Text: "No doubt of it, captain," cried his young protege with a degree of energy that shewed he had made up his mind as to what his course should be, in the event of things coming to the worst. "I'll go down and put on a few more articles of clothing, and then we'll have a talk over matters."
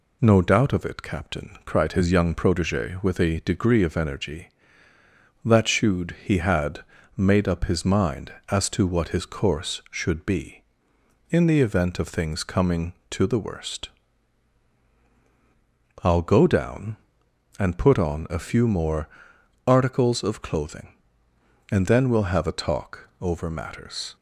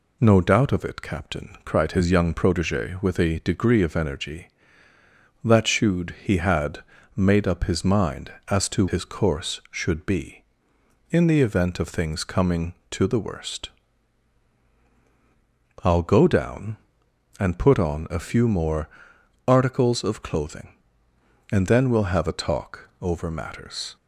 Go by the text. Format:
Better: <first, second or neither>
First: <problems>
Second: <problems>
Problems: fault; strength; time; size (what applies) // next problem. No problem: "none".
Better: first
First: pauses between "had" and "made"; slight; at 6.8 s; 0.32 s long // pauses between "more" and "articles"; noticeable; at 19.0 s; 0.60 s long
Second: pauses between "had" and "made"; slight; at 6.8 s; 0.32 s long // skips "what"; at 8.8 s // pauses between "more" and "articles"; noticeable; at 18.8 s; 0.60 s long